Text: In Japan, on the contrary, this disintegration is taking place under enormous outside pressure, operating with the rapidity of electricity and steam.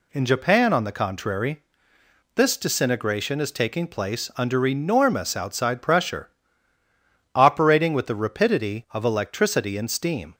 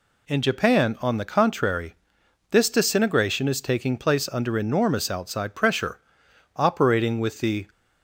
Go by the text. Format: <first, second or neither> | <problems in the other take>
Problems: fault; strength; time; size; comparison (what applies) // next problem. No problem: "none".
first | stops before "rapidity of electricity and steam"; at 7.7 s